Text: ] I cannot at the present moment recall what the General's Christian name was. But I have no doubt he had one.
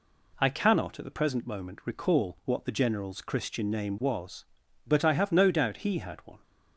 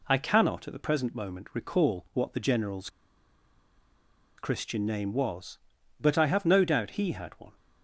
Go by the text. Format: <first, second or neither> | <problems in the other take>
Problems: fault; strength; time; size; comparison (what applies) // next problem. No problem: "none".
first | pauses between "General's" and "Christian"; strong; at 2.8 s; 1.4 s long